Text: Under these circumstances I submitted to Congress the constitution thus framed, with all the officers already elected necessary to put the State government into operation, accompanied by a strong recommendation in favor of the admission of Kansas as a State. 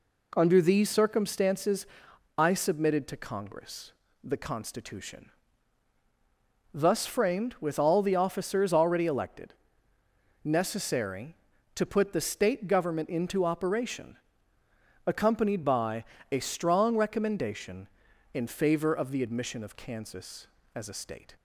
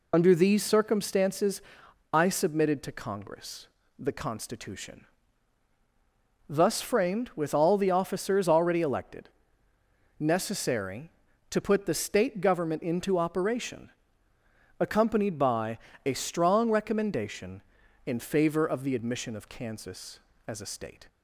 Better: first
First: pauses between "circumstances" and "I"; noticeable; at 1.8 s; 0.52 s long // pauses between "Congress" and "the"; slight; at 3.9 s; 0.32 s long // pauses between "constitution" and "thus"; strong; at 5.2 s; 1.4 s long // pauses between "elected" and "necessary"; noticeable; at 9.5 s; 0.92 s long // pauses between "by" and "a"; slight; at 16.0 s; 0.26 s long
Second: loses the start of "Under"; at 0.1 s; 75 ms // pauses between "circumstances" and "I"; noticeable; at 1.6 s; 0.52 s long // pauses between "Congress" and "the"; slight; at 3.6 s; 0.32 s long // pauses between "constitution" and "thus"; strong; at 5.0 s; 1.4 s long // pauses between "elected" and "necessary"; noticeable; at 9.2 s; 0.92 s long // pauses between "by" and "a"; slight; at 15.7 s; 0.26 s long

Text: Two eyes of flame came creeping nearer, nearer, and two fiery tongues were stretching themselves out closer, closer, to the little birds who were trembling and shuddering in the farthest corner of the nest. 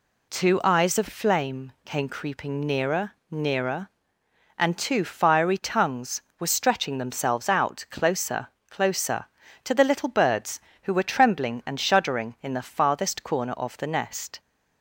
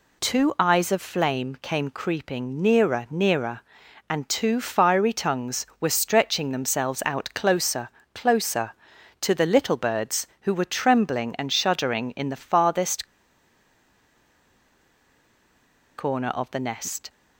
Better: first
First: none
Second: pauses between "farthest" and "corner"; strong; at 13.0 s; 2.9 s long

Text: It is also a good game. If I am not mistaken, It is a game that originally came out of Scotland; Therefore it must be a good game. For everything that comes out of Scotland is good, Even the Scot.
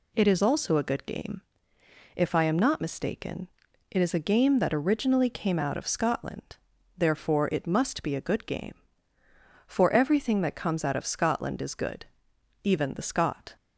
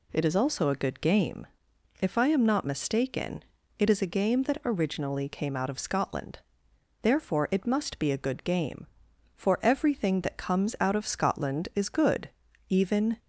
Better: first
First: none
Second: stops before "the Scot"; at 13.1 s

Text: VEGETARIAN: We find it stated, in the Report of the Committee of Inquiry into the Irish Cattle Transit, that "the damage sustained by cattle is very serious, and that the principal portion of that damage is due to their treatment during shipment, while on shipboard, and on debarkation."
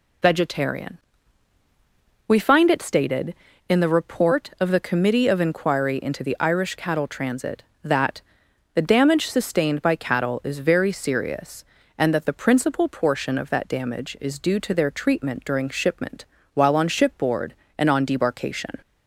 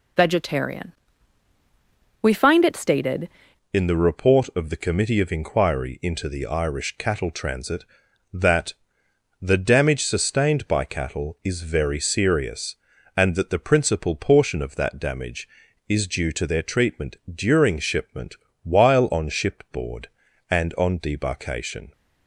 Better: first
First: pauses between "that" and "the"; noticeable; at 8.2 s; 0.52 s long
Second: changes voice at "in"; from 3.7 s on; 18.2 s long // pauses between "that" and "the"; noticeable; at 8.7 s; 0.68 s long // pauses between "treatment" and "during"; slight; at 17.1 s; 0.16 s long

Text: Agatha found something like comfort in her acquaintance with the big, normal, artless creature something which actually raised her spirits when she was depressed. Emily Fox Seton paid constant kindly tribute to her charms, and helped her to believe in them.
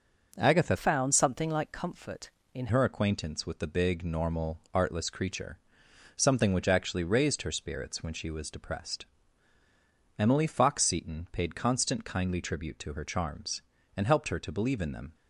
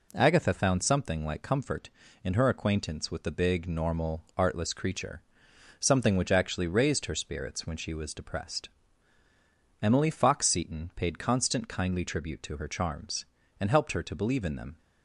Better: second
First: changes voice from "found" to "in"; from 0.7 to 2.6 s; 1.9 s long // pauses between "creature" and "something"; noticeable; at 5.5 s; 0.58 s long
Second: pauses between "creature" and "something"; noticeable; at 5.2 s; 0.58 s long

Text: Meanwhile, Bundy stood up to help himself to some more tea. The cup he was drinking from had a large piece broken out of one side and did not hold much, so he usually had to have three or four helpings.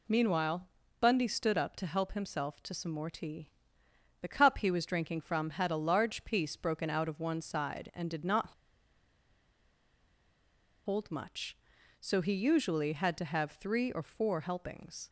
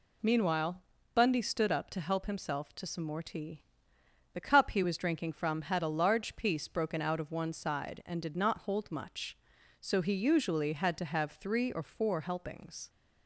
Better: second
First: pauses between "not" and "hold"; strong; at 8.5 s; 2.3 s long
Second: none

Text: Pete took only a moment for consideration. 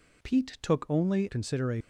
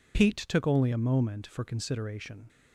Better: second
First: skips "a moment for"; at 1.2 s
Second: none

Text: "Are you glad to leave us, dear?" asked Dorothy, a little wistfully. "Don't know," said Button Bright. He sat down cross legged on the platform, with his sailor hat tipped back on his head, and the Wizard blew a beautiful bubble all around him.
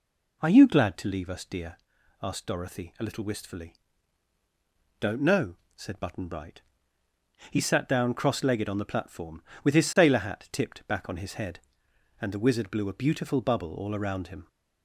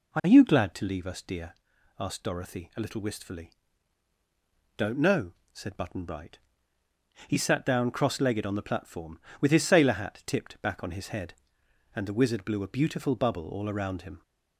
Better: neither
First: none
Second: none

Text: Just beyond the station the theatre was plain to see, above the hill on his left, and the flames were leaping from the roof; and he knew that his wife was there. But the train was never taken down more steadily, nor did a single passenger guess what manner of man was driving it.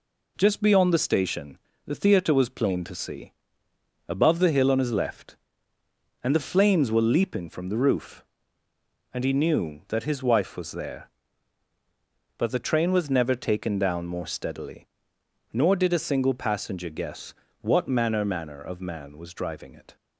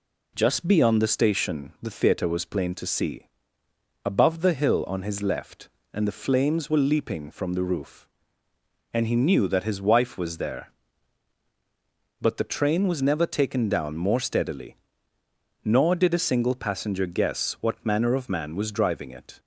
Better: second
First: pauses between "station" and "the"; slight; at 1.5 s; 0.28 s long // pauses between "guess" and "what"; slight; at 17.3 s; 0.28 s long // says "manner" twice; at 18.2 s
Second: none

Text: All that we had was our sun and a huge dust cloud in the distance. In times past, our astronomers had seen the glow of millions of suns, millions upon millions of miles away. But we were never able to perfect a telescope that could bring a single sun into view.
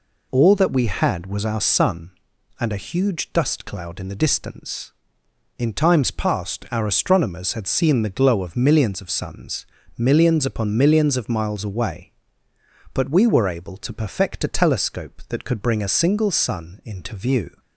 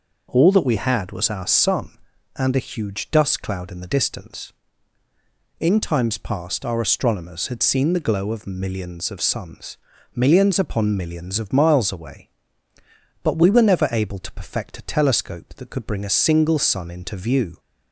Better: second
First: skips "never"; at 13.4 s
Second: none

